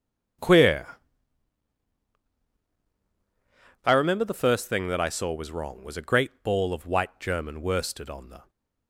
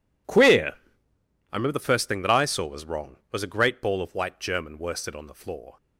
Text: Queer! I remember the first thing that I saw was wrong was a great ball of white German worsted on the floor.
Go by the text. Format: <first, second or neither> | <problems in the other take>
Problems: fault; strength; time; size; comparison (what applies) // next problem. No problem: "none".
second | starts louder than the rest; strong; until 4.3 s; 9 dB // stops before "floor"; at 8.4 s